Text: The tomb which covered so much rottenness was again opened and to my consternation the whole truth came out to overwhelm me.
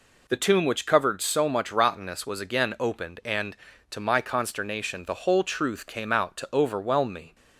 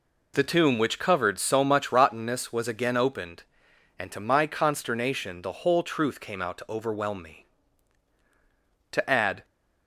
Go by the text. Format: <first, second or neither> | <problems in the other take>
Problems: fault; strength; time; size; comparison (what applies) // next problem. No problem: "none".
first | goes on to say "To add"; from 8.9 s on; 0.54 s long